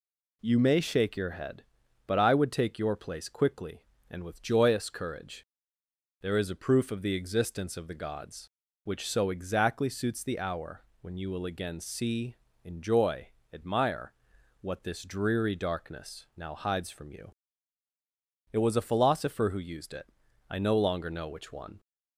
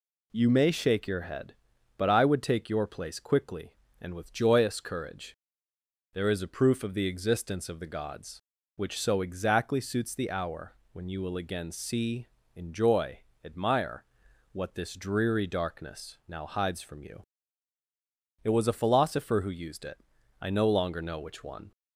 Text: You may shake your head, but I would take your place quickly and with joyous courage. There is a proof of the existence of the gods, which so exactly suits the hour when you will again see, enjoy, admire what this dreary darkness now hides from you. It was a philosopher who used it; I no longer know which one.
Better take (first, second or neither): neither